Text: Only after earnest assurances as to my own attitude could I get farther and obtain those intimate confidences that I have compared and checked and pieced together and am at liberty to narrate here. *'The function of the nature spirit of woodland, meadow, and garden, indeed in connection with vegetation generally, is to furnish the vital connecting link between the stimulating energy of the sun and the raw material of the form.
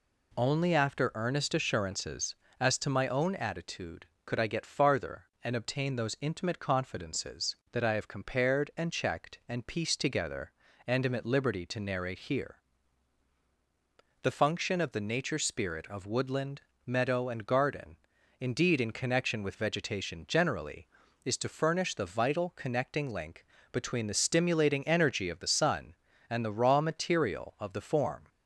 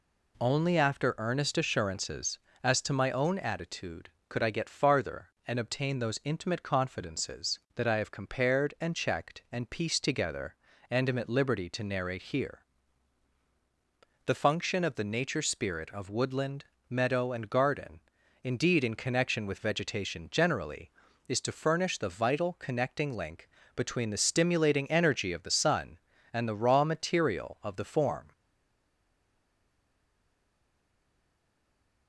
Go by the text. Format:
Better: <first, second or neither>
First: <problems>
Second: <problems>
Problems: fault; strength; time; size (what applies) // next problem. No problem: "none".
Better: first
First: pauses between "link" and "between"; slight; at 23.4 s; 0.26 s long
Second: pauses between "link" and "between"; slight; at 23.4 s; 0.26 s long // stays silent after the last word; strong; from 28.3 s on; 3.7 s long